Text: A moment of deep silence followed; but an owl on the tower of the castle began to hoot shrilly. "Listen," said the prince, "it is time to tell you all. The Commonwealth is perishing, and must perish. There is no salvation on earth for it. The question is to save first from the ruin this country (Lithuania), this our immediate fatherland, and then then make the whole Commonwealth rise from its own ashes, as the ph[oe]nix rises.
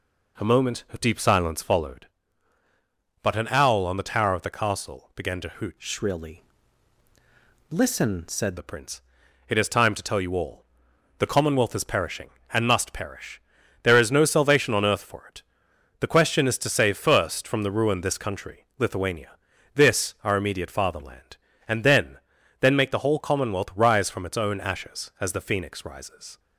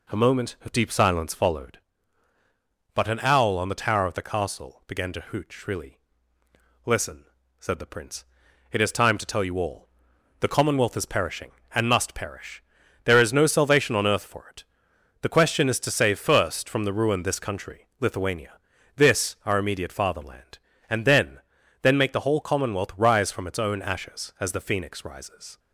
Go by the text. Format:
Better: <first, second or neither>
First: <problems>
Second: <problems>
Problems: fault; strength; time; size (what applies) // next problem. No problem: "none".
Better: second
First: changes voice from "shrilly" to "said"; from 5.7 to 8.5 s; 2.8 s long // pauses between "then" and "then"; at 22.1 s; 0.42 s long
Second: pauses between "then" and "then"; at 21.3 s; 0.42 s long